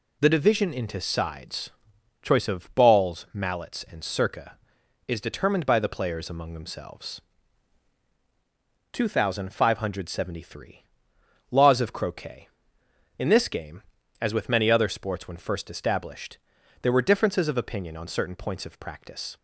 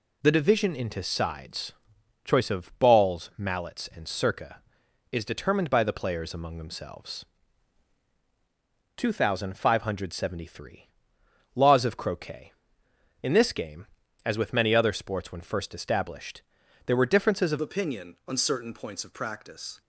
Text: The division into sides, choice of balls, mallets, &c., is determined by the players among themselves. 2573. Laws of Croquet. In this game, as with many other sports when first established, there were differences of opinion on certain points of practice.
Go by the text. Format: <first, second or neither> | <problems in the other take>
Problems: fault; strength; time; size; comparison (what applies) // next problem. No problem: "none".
first | changes voice at "opinion"; from 17.5 s on; 2.3 s long